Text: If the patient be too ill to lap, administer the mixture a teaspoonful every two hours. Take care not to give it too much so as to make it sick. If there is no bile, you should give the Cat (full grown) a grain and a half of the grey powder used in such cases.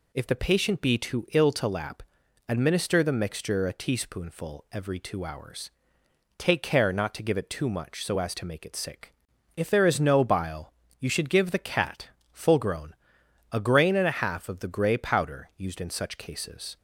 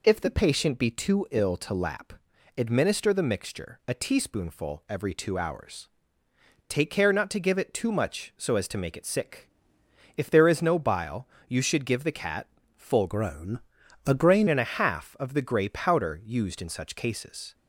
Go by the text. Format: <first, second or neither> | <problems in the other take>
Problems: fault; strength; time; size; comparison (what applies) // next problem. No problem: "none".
first | changes voice from "grown" to "grain"; from 13.0 to 14.4 s; 1.4 s long